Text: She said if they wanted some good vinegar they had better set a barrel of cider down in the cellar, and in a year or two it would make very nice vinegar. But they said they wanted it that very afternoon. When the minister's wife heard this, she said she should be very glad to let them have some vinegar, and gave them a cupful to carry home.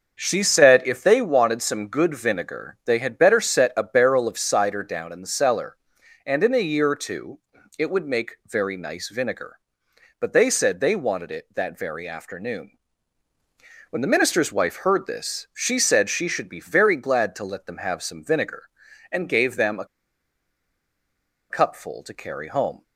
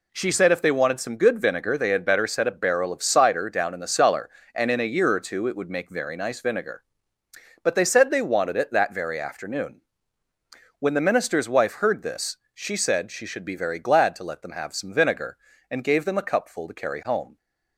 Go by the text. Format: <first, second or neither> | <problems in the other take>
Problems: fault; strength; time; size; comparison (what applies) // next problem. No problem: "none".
second | starts louder than the rest; until 1.2 s; 6.5 dB // pauses between "two" and "it"; at 7.3 s; 0.40 s long // pauses between "a" and "cupful"; strong; at 19.8 s; 1.6 s long